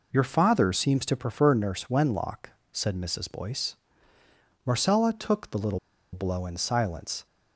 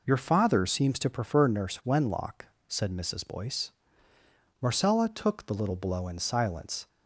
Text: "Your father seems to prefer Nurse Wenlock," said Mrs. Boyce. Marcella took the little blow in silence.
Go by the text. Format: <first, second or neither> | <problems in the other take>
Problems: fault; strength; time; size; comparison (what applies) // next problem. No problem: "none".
second | pauses between "little" and "blow"; slight; at 5.7 s; 0.34 s long